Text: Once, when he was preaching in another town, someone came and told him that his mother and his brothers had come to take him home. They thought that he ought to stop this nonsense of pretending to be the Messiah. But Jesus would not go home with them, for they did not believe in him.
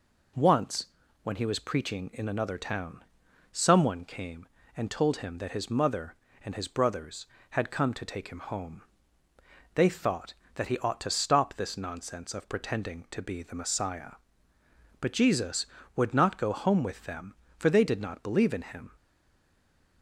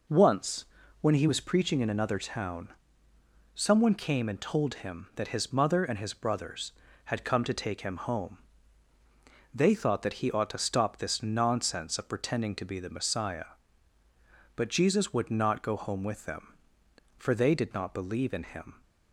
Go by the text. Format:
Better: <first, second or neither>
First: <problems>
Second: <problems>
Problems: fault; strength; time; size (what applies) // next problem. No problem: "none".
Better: second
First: stays silent after the last word; from 18.9 s on; 1.1 s long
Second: none